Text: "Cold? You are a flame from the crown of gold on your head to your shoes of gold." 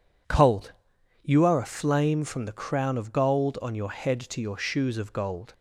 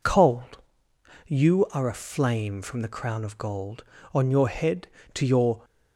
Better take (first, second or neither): first